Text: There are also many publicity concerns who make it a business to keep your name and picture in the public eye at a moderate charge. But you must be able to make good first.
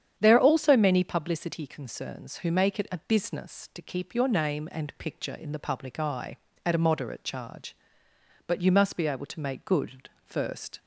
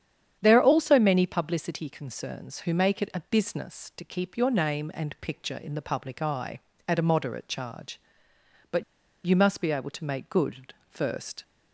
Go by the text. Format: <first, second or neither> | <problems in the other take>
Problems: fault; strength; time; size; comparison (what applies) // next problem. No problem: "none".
first | starts louder than the rest; strong; until 1.4 s; 9 dB; strong in the first // pauses between "But" and "you"; at 8.8 s; 0.42 s long